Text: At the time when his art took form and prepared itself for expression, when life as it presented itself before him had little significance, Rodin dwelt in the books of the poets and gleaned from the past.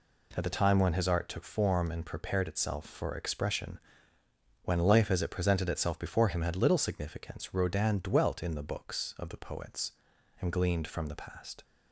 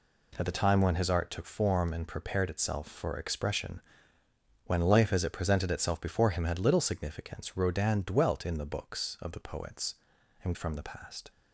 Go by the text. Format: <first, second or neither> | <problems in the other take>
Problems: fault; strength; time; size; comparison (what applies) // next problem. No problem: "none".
first | skips "gleaned"; at 10.5 s